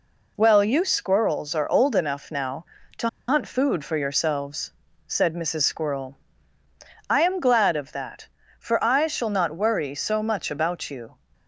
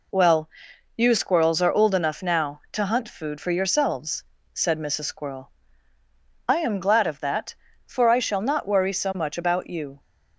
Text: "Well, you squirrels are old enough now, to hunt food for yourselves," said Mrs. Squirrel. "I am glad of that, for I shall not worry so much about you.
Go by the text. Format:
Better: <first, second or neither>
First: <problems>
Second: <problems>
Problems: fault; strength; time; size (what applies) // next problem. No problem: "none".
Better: second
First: pauses between "to" and "hunt"; slight; at 3.0 s; 0.20 s long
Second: none